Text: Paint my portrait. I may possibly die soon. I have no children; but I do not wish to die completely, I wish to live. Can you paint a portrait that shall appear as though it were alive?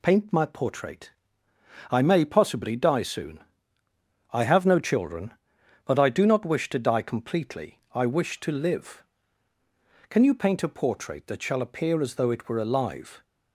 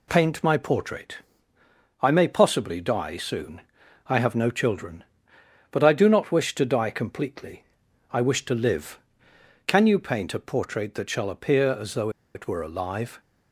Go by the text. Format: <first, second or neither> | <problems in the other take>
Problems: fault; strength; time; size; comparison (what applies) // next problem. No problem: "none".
first | pauses between "though" and "it"; slight; at 12.0 s; 0.25 s long